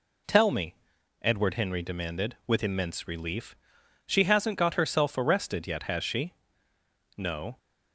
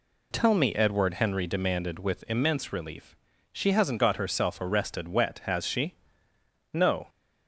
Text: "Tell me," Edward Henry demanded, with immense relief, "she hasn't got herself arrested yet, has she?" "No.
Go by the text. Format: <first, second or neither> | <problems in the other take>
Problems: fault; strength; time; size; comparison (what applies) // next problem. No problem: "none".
first | says "wet" for "yet"; at 5.0 s